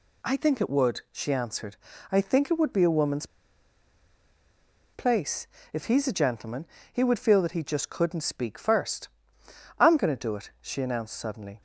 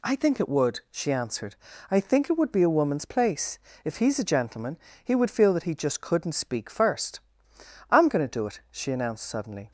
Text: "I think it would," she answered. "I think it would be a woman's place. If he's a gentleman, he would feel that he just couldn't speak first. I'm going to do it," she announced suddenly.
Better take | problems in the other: second | pauses between "woman's" and "place"; strong; at 3.2 s; 1.6 s long

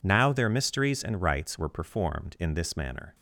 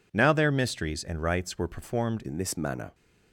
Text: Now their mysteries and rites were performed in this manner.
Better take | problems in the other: first | changes voice at "in"; from 2.2 s on; 0.7 s long

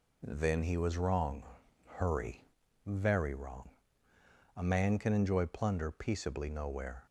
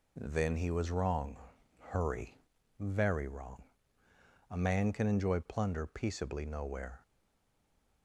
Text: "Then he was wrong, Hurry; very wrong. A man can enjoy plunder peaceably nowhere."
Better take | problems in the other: first | stays silent after the last word; from 7.0 s on; 1.0 s long

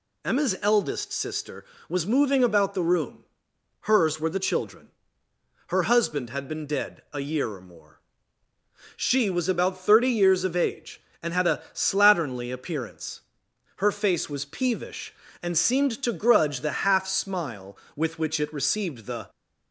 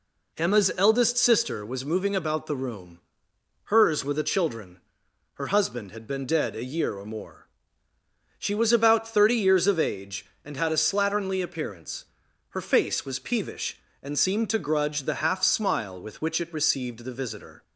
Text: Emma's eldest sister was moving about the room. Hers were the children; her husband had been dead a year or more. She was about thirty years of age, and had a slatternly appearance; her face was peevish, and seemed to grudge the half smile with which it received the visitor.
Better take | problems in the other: second | stops before "visitor"; at 19.2 s

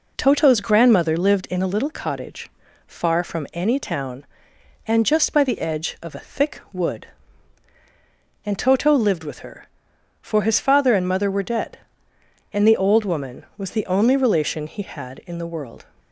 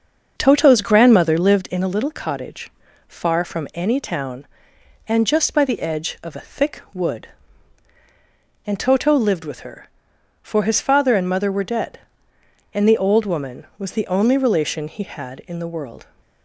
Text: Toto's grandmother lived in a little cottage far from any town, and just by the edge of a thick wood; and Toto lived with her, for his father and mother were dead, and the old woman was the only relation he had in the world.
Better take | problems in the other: first | starts louder than the rest; until 1.6 s; 6.5 dB // pauses between "cottage" and "far"; at 2.7 s; 0.38 s long; also in the first

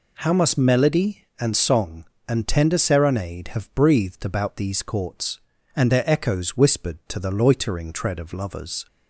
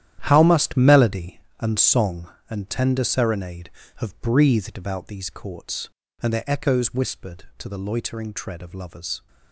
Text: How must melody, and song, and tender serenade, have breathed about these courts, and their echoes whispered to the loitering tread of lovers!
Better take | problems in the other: first | gets quieter; strong; throughout; 12 dB

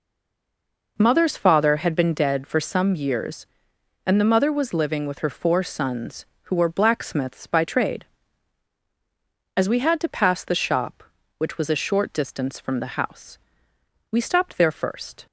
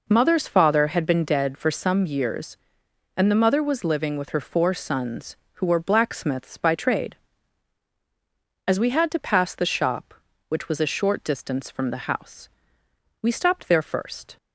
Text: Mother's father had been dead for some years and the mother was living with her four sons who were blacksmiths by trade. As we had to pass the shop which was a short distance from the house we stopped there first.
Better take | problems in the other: second | stays silent before the first word; until 0.9 s; 0.9 s long // pauses between "house" and "we"; noticeable; at 13.3 s; 0.74 s long; noticeable in the second

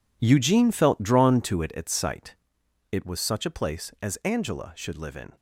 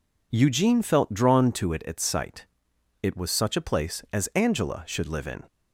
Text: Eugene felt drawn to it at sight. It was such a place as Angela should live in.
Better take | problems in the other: second | gets quieter; strong; throughout; 13.5 dB

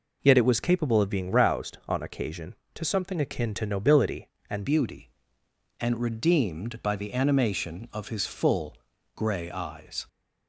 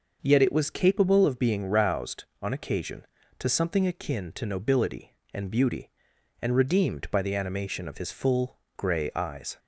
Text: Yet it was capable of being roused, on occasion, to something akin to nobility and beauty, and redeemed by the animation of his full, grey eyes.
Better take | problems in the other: second | changes voice at "beauty"; from 4.6 s on; 5.4 s long

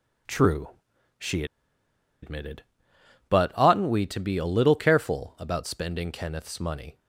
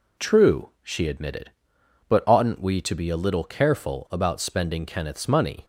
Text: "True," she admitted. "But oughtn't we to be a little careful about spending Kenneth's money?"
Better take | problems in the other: second | pauses between "she" and "admitted"; noticeable; at 1.4 s; 0.78 s long

